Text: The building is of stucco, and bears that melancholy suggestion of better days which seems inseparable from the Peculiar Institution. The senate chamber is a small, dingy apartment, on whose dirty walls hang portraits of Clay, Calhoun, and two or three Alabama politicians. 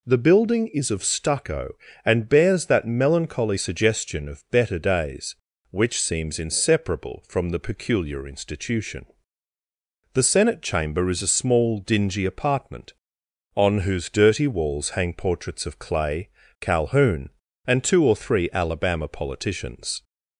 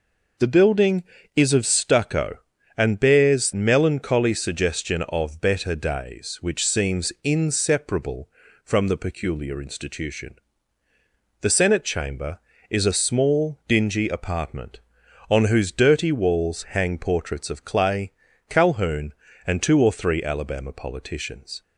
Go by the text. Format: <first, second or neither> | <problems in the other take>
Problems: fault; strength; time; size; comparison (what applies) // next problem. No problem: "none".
first | skips "that"; at 3.5 s